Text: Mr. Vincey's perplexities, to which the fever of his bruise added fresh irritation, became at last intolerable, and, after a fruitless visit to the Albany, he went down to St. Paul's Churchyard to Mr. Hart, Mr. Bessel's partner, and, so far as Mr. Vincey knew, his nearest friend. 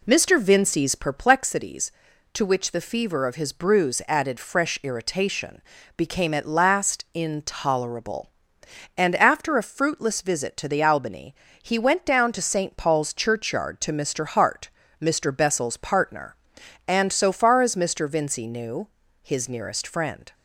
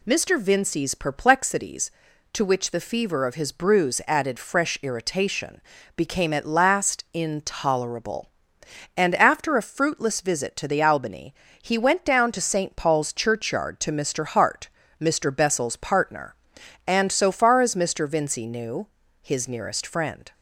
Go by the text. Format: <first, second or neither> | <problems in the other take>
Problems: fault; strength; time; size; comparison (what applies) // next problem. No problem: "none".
second | starts louder than the rest; slight; until 1.2 s; 2 dB